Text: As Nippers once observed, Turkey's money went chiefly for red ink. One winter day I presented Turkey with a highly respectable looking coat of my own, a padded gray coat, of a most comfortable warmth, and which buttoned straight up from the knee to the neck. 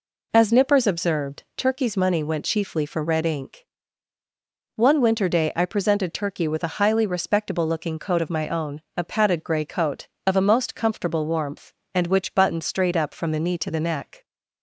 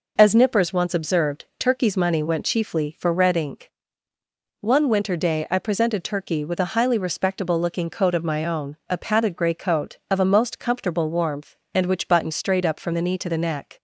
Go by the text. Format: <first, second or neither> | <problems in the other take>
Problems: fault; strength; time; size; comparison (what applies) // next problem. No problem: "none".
second | skips "once"; at 0.8 s